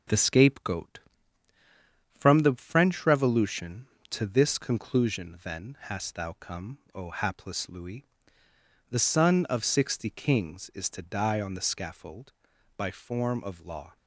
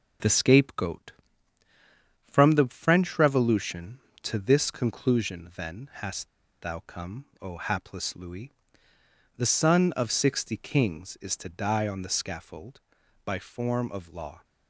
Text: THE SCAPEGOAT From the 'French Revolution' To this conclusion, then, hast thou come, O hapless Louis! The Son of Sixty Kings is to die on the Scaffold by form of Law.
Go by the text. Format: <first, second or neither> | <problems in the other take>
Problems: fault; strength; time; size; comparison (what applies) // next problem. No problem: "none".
first | pauses between "hast" and "thou"; slight; at 6.2 s; 0.32 s long